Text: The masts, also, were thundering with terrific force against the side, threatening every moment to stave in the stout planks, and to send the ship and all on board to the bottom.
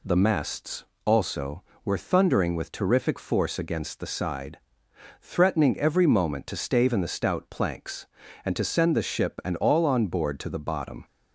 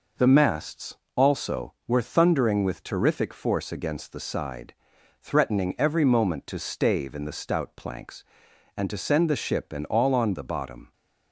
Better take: first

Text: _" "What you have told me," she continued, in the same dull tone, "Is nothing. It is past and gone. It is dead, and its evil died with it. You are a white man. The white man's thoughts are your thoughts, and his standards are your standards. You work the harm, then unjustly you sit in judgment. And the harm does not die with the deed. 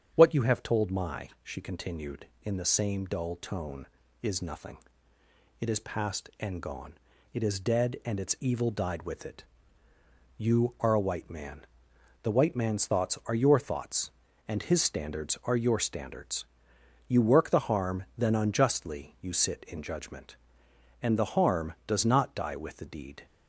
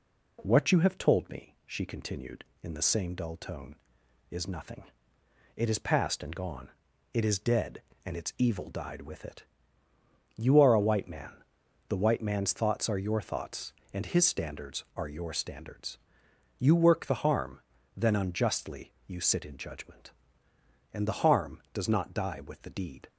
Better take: second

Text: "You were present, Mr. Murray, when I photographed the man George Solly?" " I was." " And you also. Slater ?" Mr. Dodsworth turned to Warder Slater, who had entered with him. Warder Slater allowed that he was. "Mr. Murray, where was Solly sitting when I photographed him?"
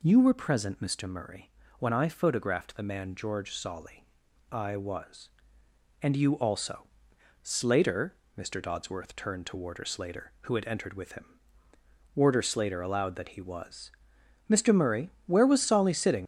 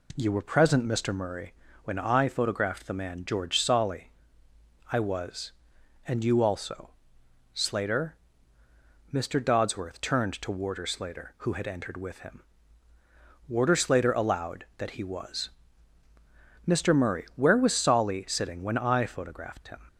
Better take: second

